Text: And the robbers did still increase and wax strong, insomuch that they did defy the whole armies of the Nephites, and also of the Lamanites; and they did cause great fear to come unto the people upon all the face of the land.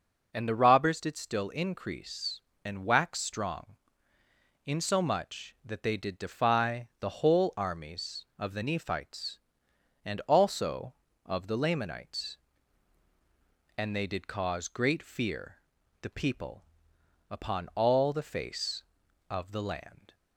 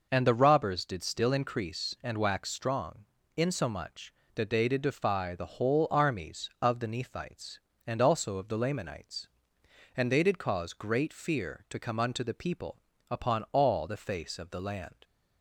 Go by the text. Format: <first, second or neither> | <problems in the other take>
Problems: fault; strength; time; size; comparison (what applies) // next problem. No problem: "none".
second | skips "to come unto"; at 15.7 s // pauses between "people" and "upon"; noticeable; at 16.6 s; 0.66 s long; slight in the second